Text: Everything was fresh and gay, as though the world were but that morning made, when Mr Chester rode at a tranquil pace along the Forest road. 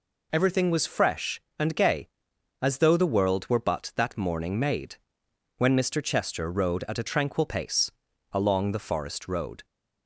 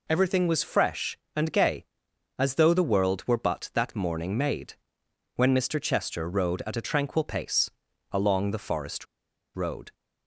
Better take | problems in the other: first | pauses between "pace" and "along"; at 7.6 s; 0.42 s long; also in the first // pauses between "Forest" and "road"; noticeable; at 9.0 s; 0.50 s long

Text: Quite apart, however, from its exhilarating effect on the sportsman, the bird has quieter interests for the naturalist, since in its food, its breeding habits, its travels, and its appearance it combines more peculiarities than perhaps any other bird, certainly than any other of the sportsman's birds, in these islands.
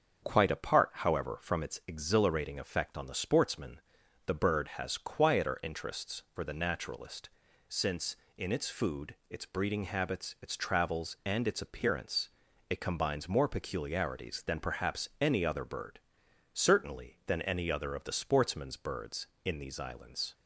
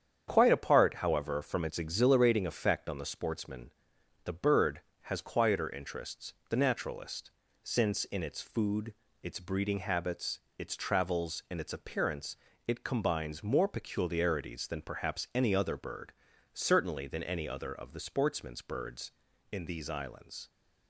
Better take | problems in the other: first | starts louder than the rest; strong; until 1.3 s; 8 dB; also in the first // skips "for"; at 6.4 s // pauses between "appearance" and "it"; slight; at 12.3 s; 0.30 s long; also in the first

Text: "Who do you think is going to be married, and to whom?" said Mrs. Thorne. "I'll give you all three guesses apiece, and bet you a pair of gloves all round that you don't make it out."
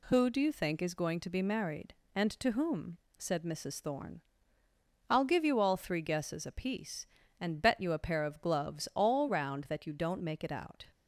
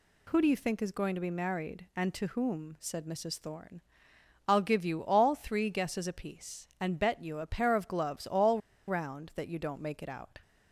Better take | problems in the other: first | pauses between "all" and "round"; slight; at 8.5 s; 0.27 s long

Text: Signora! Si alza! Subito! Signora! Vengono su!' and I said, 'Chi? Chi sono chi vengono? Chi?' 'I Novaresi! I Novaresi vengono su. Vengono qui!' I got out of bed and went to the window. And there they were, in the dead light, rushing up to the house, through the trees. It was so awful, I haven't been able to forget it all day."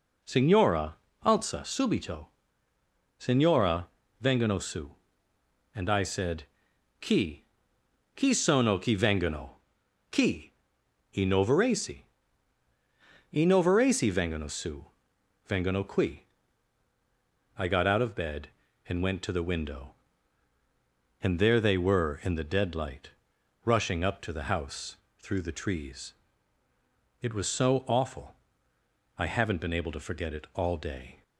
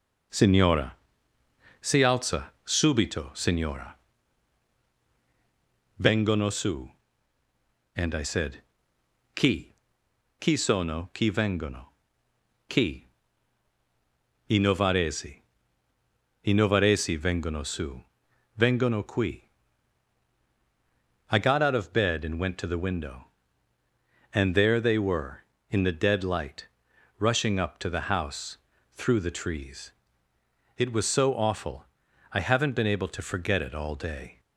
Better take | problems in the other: second | skips "Si"; at 1.1 s

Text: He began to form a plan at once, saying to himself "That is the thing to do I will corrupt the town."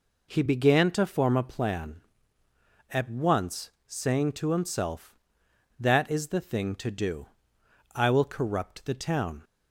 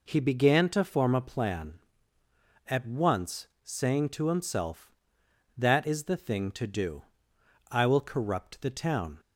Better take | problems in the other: neither | pauses between "do" and "I"; noticeable; the same in both

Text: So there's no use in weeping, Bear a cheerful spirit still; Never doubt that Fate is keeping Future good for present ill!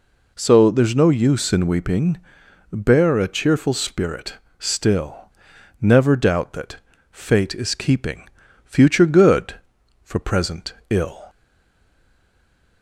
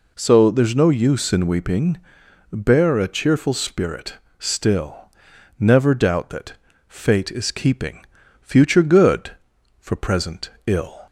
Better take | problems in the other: second | pauses between "spirit" and "still"; slight; at 4.3 s; 0.24 s long; slight in the second // pauses between "that" and "Fate"; slight; at 6.7 s; 0.34 s long; slight in the second // pauses between "keeping" and "Future"; slight; at 8.2 s; 0.36 s long; slight in the second // pauses between "present" and "ill"; slight; at 10.7 s; 0.16 s long; slight in the second // stays silent after the last word; noticeable; from 11.2 s on; 1.6 s long

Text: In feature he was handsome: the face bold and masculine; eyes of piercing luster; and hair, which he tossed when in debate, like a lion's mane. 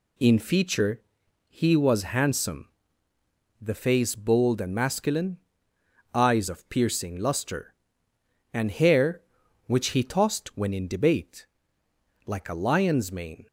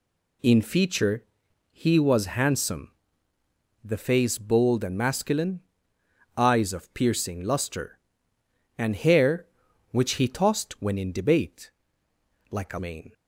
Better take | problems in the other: first | pauses between "feature" and "he"; noticeable; at 1.2 s; 0.48 s long; noticeable in the first // skips "lion's"; at 12.7 s

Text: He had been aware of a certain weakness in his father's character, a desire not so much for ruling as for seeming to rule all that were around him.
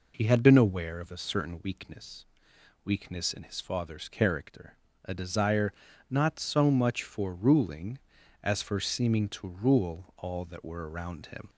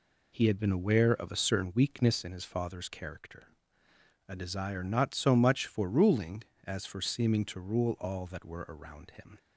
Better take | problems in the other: second | says "weakness" twice; at 2.8 s // pauses between "desire" and "not"; slight; at 5.7 s; 0.36 s long

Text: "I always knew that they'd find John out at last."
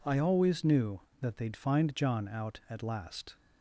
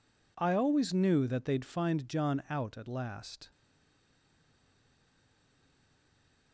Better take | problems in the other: first | stays silent after the last word; strong; from 3.5 s on; 3.0 s long

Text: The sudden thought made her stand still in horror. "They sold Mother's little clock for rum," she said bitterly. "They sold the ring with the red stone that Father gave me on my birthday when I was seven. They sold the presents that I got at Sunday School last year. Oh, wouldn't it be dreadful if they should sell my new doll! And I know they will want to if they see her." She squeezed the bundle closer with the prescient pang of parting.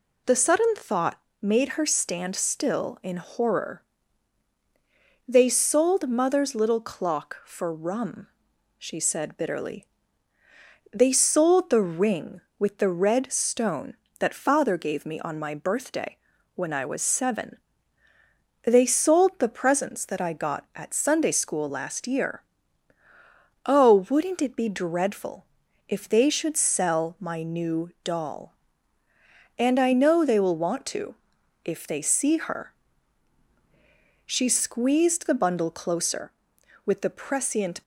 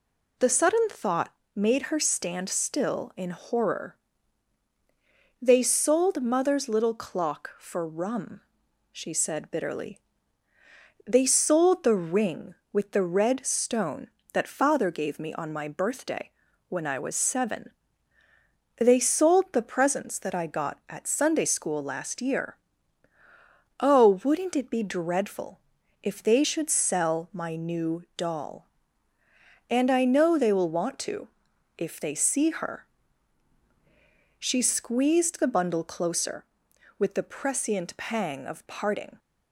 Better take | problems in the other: second | pauses between "thought" and "made"; slight; at 1.1 s; 0.22 s long; slight in the second // pauses between "birthday" and "when"; at 16.1 s; 0.38 s long; also in the second // pauses between "dreadful" and "if"; at 25.4 s; 0.44 s long; also in the second // pauses between "to" and "if"; noticeable; at 31.1 s; 0.48 s long; noticeable in the second // stops before "pang of parting"; at 37.8 s

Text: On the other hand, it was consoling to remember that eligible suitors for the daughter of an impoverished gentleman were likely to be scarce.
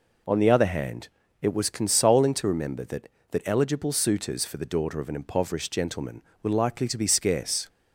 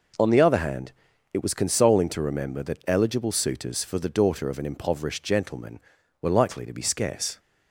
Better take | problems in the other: second | says "that" twice; at 3.3 s

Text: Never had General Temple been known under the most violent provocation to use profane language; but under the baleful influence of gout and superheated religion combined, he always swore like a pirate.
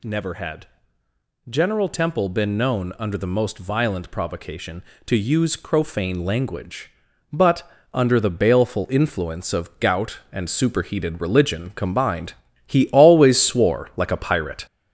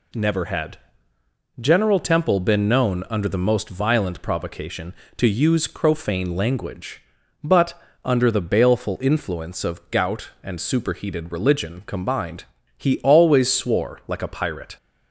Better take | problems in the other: second | gets louder; noticeable; throughout; 4 dB // pauses between "had" and "General"; noticeable; at 0.6 s; 0.82 s long; noticeable in the second // pauses between "but" and "under"; slight; at 7.6 s; 0.24 s long; slight in the second

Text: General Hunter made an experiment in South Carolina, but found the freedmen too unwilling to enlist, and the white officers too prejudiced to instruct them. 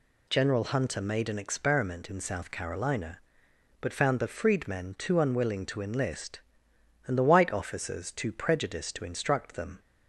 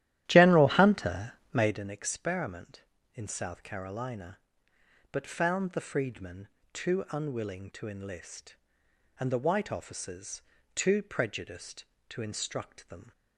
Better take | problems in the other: first | starts louder than the rest; strong; until 1.8 s; 12.5 dB // pauses between "Hunter" and "made"; slight; at 1.3 s; 0.20 s long // pauses between "freedmen" and "too"; slight; at 6.4 s; 0.26 s long // pauses between "officers" and "too"; slight; at 10.4 s; 0.32 s long

